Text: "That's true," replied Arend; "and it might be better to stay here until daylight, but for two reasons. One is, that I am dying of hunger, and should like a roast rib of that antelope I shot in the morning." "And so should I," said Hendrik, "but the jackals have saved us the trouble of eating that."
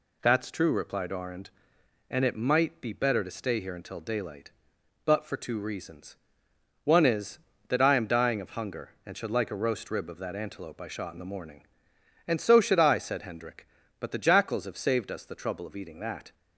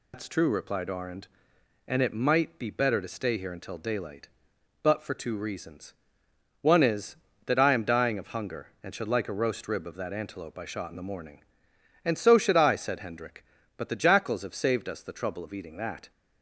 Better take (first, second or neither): first